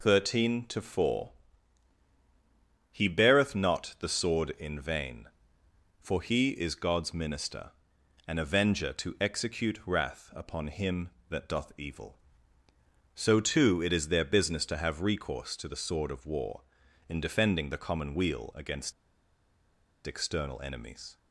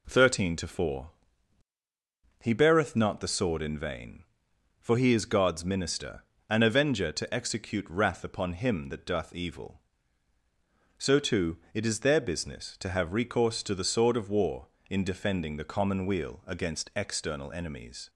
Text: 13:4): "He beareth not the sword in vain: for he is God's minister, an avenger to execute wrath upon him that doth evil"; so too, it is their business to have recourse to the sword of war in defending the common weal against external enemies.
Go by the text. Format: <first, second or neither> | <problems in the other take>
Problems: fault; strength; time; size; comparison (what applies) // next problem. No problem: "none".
second | pauses between "against" and "external"; at 18.9 s; 1.1 s long